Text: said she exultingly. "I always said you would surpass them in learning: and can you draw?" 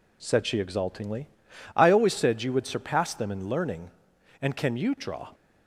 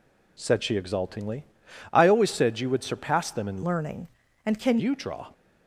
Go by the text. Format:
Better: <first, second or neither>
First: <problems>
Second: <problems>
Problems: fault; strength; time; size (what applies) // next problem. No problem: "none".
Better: first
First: none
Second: changes voice from "learning" to "can"; from 3.6 to 4.7 s; 1.1 s long